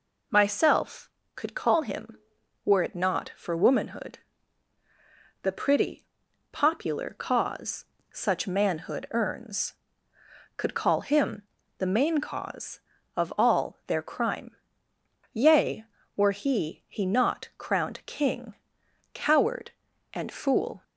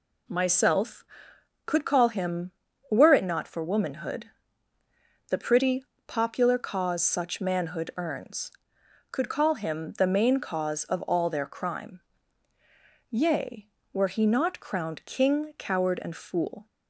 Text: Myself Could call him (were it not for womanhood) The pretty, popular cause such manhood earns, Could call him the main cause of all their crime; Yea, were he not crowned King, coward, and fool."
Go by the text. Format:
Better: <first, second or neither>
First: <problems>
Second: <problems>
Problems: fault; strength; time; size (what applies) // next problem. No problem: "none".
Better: second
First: pauses between "cause" and "such"; slight; at 7.8 s; 0.28 s long // pauses between "him" and "the"; slight; at 11.4 s; 0.34 s long // says "he" twice; at 16.8 s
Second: none